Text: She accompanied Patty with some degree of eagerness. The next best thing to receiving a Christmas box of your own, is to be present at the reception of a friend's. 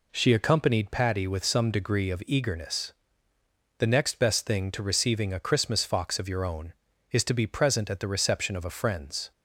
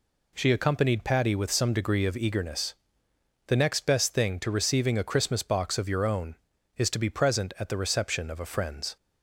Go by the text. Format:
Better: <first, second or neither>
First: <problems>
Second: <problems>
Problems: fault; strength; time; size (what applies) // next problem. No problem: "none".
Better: second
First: says "fox" for "box"; at 5.8 s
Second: none